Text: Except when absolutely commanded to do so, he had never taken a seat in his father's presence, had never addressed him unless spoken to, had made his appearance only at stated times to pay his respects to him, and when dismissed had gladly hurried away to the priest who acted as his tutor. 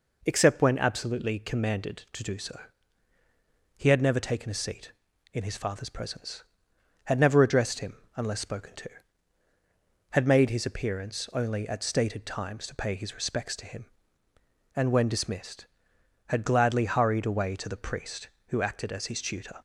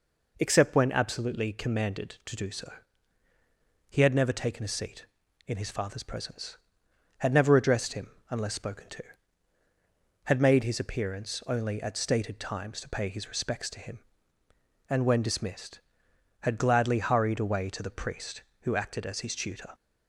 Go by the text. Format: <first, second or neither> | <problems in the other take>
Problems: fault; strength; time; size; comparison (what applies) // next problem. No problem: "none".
neither | pauses between "him" and "unless"; slight; the same in both